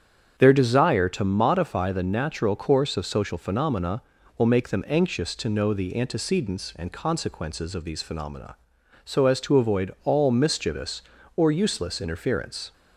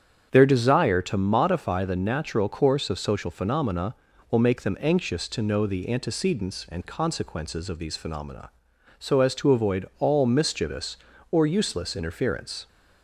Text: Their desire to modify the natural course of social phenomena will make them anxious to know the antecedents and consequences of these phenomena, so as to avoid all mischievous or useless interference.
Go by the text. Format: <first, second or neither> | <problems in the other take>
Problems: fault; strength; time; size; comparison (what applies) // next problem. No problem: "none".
neither | starts louder than the rest; strong; the same in both